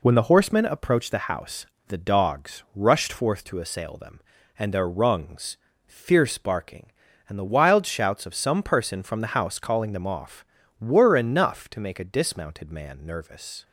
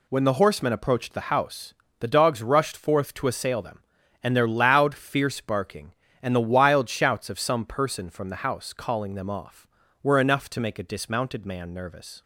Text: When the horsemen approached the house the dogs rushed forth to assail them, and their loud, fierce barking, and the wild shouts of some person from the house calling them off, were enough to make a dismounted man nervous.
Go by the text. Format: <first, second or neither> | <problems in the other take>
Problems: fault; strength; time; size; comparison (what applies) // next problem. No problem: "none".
second | pauses between "house" and "the"; slight; at 1.6 s; 0.22 s long; slight in the second // says "rungs" for "loud"; at 4.8 s